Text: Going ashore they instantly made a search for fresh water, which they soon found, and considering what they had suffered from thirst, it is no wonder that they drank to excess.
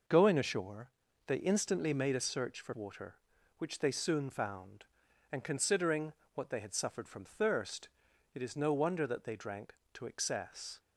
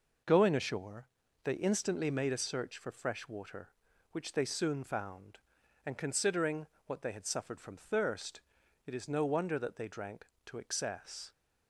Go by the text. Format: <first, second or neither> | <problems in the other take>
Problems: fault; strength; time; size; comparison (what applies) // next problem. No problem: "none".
second | pauses between "ashore" and "they"; slight; at 0.9 s; 0.36 s long; slight in the second // skips "fresh"; at 2.7 s // pauses between "considering" and "what"; slight; at 6.1 s; 0.22 s long; slight in the second